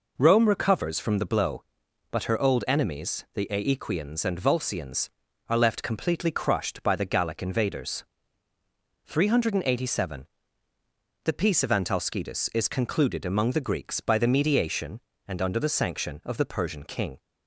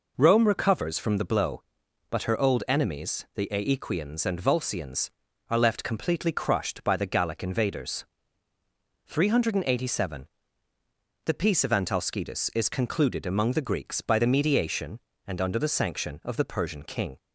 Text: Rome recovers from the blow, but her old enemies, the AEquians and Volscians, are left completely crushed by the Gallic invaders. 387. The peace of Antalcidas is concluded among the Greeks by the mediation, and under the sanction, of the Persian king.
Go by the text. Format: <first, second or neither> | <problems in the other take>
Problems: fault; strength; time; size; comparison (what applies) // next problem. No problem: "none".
neither | none